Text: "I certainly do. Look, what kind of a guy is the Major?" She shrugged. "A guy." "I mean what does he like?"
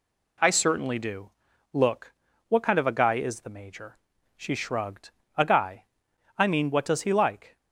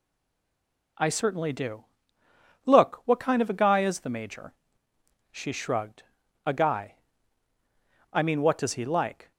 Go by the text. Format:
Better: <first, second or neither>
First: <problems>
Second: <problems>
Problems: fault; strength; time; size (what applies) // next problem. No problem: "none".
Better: first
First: none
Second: stays silent before the first word; slight; until 0.9 s; 0.9 s long